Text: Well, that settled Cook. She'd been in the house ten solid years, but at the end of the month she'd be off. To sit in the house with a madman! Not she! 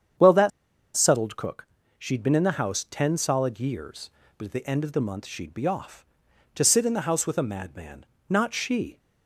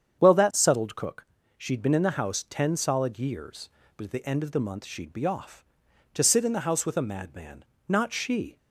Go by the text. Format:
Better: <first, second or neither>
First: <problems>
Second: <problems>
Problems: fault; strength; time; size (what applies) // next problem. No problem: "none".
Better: second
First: starts louder than the rest; strong; until 1.6 s; 8 dB // pauses between "that" and "settled"; noticeable; at 0.5 s; 0.46 s long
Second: starts louder than the rest; strong; until 1.2 s; 8 dB